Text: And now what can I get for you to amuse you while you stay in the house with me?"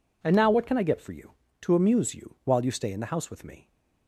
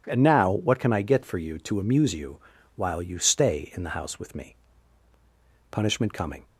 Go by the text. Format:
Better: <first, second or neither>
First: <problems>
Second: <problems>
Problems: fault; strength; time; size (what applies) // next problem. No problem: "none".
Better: first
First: none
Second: pauses between "you" and "while"; slight; at 2.3 s; 0.36 s long // goes on to say "Punishment coming"; noticeable; from 5.7 s on; 0.74 s long